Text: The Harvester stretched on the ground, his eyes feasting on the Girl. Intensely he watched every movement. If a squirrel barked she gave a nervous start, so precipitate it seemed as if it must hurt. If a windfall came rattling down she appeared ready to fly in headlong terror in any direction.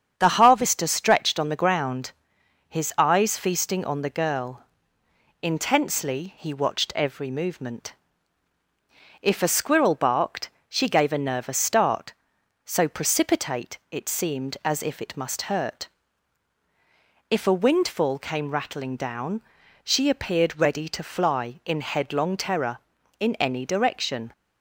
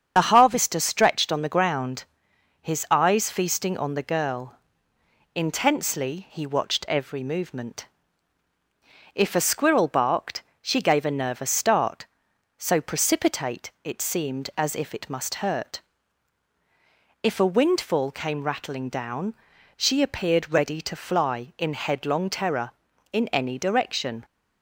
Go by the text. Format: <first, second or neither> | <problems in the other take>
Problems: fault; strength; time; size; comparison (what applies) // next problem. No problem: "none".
first | loses the start of "The"; at 0.1 s; 50 ms // starts louder than the rest; strong; until 1.1 s; 7.5 dB; strong in the first // pauses between "barked" and "she"; slight; at 10.4 s; 0.22 s long; slight in the first // pauses between "down" and "she"; at 19.3 s; 0.42 s long; also in the first